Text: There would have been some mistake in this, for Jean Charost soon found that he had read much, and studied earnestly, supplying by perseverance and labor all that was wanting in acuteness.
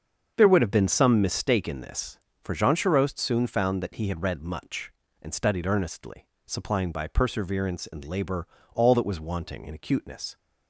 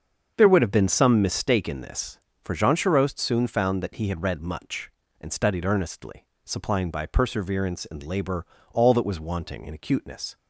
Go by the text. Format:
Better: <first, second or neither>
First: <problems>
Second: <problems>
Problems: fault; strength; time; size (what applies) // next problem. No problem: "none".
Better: neither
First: starts louder than the rest; until 1.3 s; 7 dB // pauses between "labor" and "all"; slight; at 8.4 s; 0.26 s long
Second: starts louder than the rest; until 1.3 s; 7 dB // pauses between "labor" and "all"; slight; at 8.4 s; 0.26 s long